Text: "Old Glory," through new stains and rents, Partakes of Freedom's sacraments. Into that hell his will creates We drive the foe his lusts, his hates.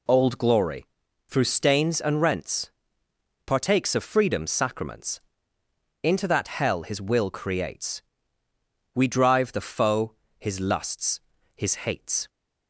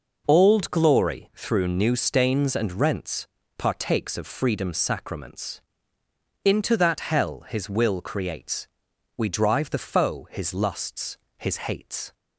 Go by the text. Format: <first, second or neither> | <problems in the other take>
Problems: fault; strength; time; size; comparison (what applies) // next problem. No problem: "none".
second | skips "new"; at 1.4 s // pauses between "creates" and "We"; noticeable; at 8.0 s; 0.94 s long; noticeable in the second // pauses between "foe" and "his"; slight; at 10.1 s; 0.26 s long